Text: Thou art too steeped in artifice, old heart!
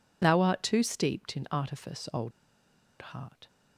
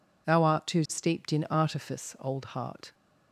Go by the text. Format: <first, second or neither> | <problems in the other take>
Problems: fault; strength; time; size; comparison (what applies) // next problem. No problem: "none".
second | pauses between "old" and "heart"; noticeable; at 2.3 s; 0.83 s long